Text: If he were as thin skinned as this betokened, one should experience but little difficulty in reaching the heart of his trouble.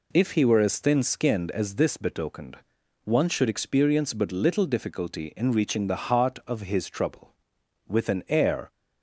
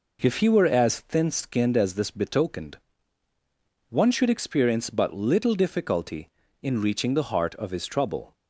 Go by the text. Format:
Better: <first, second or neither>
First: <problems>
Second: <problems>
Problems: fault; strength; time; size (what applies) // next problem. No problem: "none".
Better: second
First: goes on to say "With an air"; noticeable; from 7.8 s on; 0.84 s long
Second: none